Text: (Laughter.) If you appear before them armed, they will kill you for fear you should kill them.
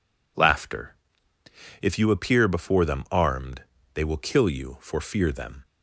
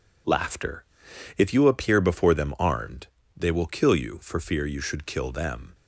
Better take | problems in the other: second | skips "you should kill"; at 5.3 s

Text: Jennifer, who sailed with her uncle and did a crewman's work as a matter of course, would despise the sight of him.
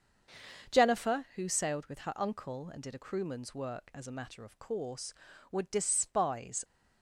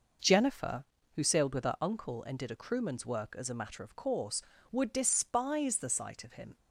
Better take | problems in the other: second | starts louder than the rest; until 1.7 s; 6.5 dB // stops before "the sight of him"; at 6.6 s

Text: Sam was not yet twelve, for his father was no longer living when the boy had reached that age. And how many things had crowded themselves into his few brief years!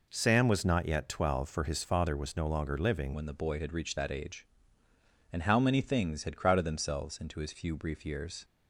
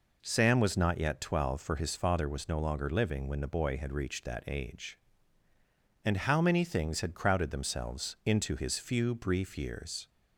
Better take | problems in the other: second | changes voice at "when"; from 3.1 s on; 5.3 s long

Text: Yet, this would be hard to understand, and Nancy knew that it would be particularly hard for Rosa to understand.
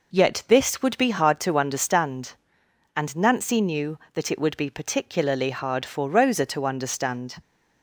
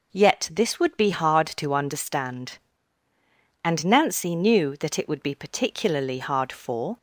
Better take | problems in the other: first | stops before "Rosa to understand"; at 6.9 s

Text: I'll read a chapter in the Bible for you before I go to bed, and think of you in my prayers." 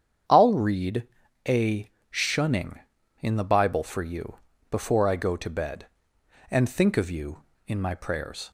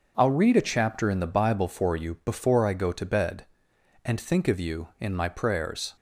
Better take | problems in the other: second | starts louder than the rest; strong; until 1.6 s; 8 dB // pauses between "read" and "a"; at 1.0 s; 0.40 s long // says "shunning" for "chapter"; at 2.1 s // pauses between "you" and "before"; slight; at 4.3 s; 0.36 s long

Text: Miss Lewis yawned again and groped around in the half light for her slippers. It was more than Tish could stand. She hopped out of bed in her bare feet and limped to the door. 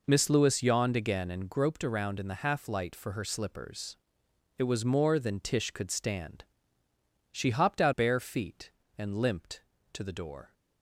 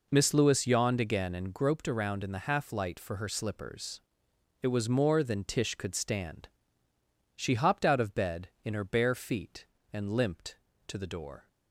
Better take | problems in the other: second | skips "of bed in her"; at 7.9 s

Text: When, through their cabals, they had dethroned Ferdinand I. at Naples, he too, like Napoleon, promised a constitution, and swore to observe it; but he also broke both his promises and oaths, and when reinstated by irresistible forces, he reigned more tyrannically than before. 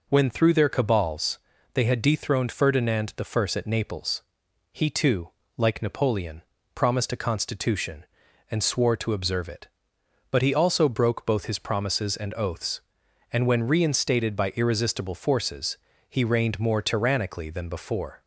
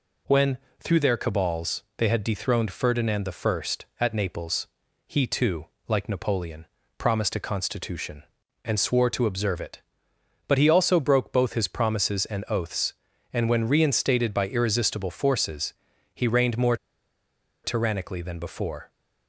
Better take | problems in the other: first | pauses between "more" and "tyrannically"; noticeable; at 16.7 s; 0.88 s long

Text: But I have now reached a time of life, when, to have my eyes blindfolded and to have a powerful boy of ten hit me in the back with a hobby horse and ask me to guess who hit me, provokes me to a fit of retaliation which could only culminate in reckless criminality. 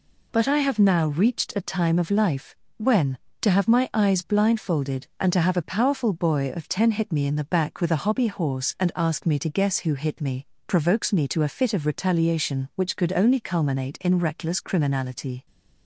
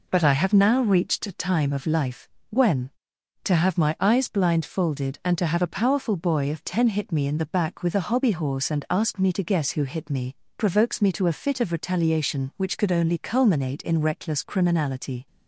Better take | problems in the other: neither | none

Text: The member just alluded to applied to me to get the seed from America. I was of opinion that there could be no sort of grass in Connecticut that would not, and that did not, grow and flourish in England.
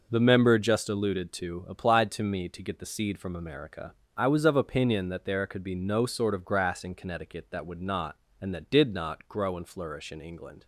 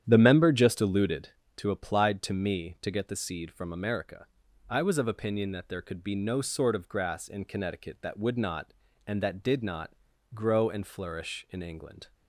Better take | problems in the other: first | starts louder than the rest; strong; until 1.3 s; 9.5 dB

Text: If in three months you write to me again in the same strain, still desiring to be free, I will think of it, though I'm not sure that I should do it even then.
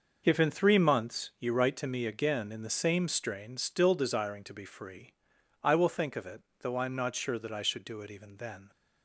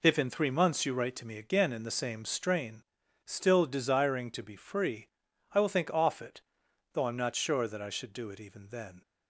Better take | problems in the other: first | says "off" for "of"; at 5.9 s

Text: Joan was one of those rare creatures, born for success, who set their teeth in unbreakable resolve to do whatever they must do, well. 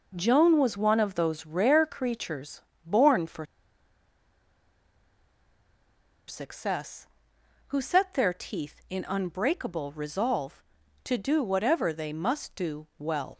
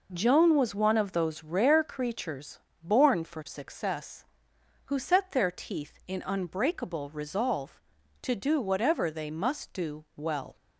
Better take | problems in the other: second | pauses between "for" and "success"; strong; at 3.4 s; 2.8 s long

